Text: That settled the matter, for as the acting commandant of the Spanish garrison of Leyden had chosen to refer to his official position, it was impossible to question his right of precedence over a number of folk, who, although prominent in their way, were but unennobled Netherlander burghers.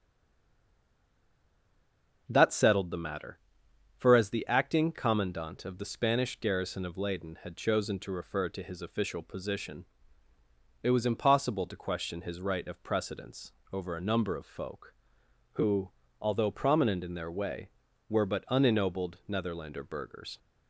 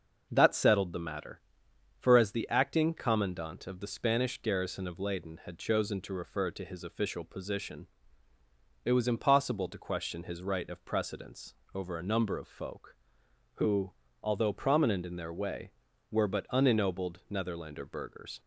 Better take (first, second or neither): second